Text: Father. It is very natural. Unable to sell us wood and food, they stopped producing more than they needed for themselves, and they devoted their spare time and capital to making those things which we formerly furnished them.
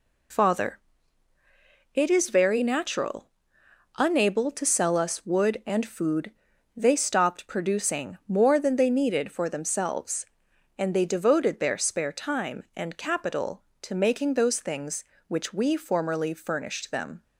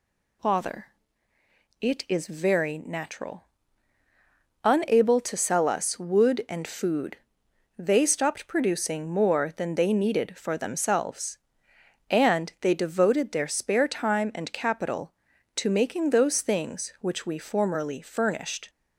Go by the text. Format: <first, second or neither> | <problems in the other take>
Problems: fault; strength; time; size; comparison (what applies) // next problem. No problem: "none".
first | stops before "them"; at 18.6 s